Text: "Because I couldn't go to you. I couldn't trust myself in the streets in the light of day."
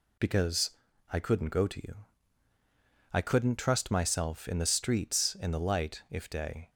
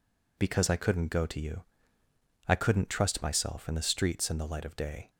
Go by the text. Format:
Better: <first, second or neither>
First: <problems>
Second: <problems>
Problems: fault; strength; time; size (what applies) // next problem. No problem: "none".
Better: second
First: pauses between "Because" and "I"; at 0.6 s; 0.42 s long // says "if" for "of"; at 6.0 s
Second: none